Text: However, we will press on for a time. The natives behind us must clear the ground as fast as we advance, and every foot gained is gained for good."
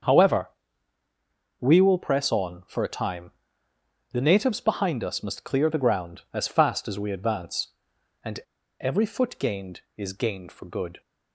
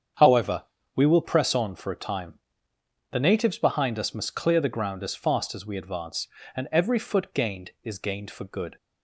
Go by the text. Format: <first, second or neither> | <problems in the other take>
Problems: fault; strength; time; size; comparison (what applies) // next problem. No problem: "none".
second | starts louder than the rest; until 2.1 s; 7 dB; strong in the second // pauses between "and" and "every"; at 8.3 s; 0.40 s long